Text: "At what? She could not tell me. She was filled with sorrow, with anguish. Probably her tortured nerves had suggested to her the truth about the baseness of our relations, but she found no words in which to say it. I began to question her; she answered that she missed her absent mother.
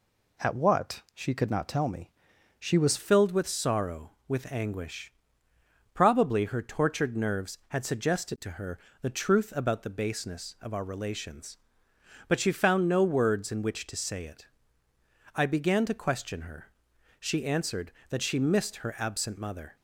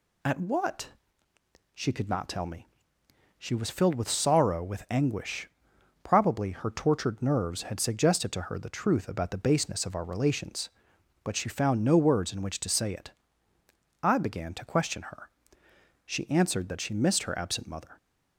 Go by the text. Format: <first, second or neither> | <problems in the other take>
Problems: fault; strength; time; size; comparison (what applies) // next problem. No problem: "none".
second | changes voice at "filled"; from 2.9 s on; 16.8 s long // pauses between "her" and "the"; slight; at 8.7 s; 0.22 s long